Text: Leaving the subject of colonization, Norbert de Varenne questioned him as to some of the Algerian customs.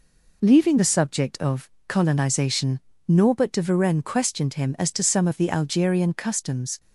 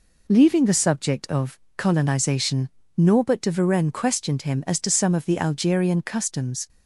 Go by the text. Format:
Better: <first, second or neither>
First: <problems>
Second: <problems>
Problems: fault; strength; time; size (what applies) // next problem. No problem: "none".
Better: neither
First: pauses between "of" and "colonization"; slight; at 1.6 s; 0.18 s long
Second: pauses between "of" and "colonization"; slight; at 1.5 s; 0.18 s long